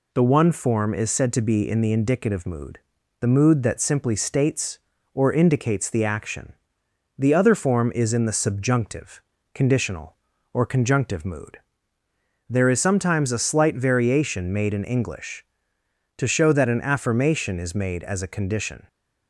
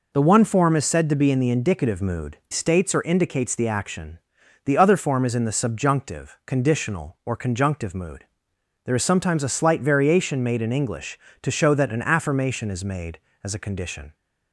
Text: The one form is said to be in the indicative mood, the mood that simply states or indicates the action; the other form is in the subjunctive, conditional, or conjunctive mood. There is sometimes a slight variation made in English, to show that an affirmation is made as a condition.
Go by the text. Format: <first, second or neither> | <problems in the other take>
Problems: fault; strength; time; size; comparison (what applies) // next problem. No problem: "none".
first | skips "the mood that simply"; at 2.4 s